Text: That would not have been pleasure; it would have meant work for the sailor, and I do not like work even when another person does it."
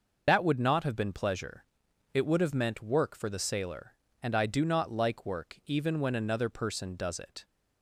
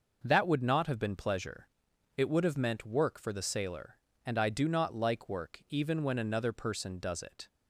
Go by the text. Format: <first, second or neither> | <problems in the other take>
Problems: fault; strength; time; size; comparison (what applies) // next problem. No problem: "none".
second | loses the start of "That"; at 0.2 s; 75 ms